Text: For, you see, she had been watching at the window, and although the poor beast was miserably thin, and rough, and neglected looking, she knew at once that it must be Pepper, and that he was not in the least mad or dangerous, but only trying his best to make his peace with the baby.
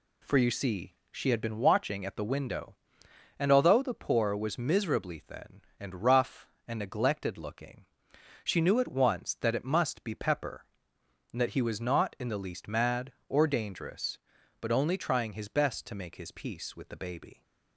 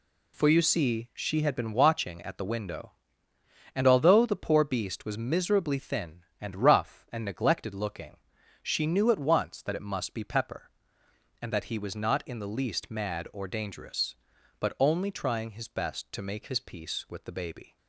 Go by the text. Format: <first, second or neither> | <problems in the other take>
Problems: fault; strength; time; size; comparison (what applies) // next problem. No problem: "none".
second | skips "beast"; at 4.3 s